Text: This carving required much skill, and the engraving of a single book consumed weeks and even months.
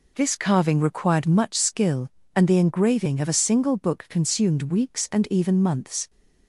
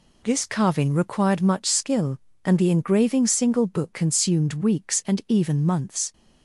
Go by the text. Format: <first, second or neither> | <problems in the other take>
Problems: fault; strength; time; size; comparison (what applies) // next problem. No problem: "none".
first | skips "of a"; at 3.2 s